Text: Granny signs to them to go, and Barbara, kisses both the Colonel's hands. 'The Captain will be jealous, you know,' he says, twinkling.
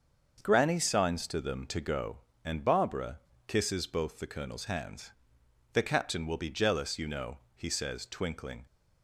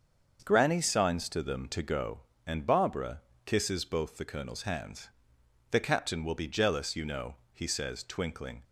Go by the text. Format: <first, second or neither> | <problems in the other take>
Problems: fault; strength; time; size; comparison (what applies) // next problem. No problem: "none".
neither | starts louder than the rest; the same in both